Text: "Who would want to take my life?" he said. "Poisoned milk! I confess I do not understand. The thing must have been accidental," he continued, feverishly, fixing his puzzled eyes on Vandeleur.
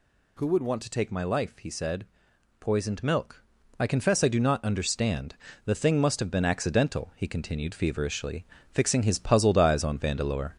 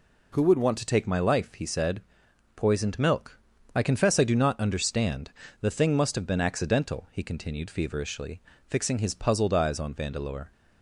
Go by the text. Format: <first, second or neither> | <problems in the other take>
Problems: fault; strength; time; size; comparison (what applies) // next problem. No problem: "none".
second | gets louder; slight; throughout; 3 dB